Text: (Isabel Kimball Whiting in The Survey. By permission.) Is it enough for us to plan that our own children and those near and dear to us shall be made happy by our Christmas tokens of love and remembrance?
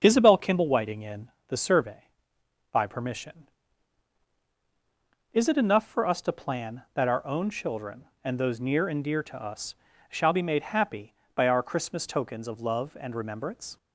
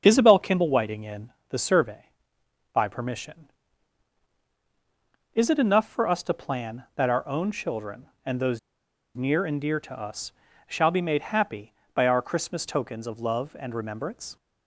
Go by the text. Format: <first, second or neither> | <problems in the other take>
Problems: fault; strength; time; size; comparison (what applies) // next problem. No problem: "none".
first | starts louder than the rest; until 1.0 s; 6.5 dB; also in the first // pauses between "in" and "The"; slight; at 1.3 s; 0.16 s long; slight in the first // pauses between "those" and "near"; noticeable; at 8.5 s; 0.56 s long // pauses between "us" and "shall"; slight; at 10.3 s; 0.36 s long; slight in the first